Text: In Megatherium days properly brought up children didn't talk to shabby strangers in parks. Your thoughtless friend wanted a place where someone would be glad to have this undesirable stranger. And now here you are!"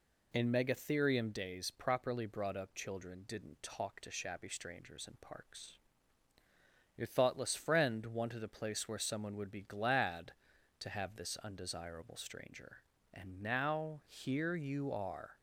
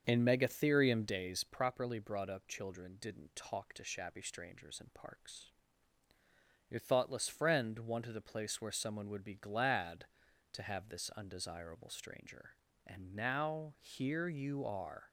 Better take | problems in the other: first | starts louder than the rest; until 1.5 s; 6.5 dB

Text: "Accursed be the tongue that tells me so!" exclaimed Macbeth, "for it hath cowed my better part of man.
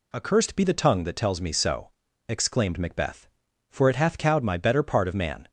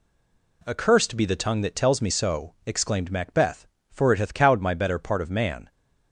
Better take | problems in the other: first | stays silent before the first word; slight; until 0.6 s; 0.6 s long

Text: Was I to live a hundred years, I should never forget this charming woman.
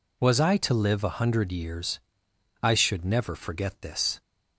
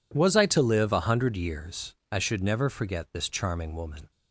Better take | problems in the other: second | stops before "charming woman"; at 4.2 s

